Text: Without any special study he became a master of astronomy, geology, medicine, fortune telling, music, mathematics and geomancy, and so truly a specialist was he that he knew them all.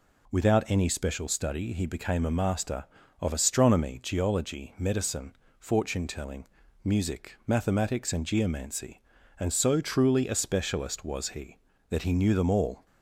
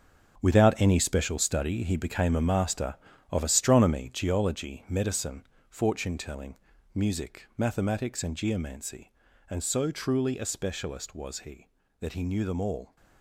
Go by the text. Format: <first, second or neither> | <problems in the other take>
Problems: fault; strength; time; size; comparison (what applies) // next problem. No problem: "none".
first | gets quieter; strong; throughout; 11 dB